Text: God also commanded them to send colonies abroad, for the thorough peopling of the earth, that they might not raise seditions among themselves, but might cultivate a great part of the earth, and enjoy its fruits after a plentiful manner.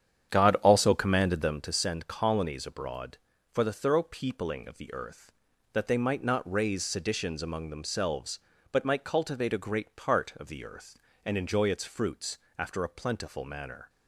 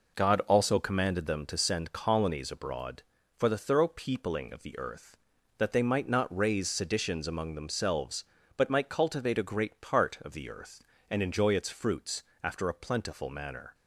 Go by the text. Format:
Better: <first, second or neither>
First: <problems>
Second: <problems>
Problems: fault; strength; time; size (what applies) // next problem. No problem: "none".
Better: second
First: starts louder than the rest; strong; until 1.7 s; 9 dB // pauses between "fruits" and "after"; slight; at 12.3 s; 0.22 s long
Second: pauses between "fruits" and "after"; slight; at 12.2 s; 0.22 s long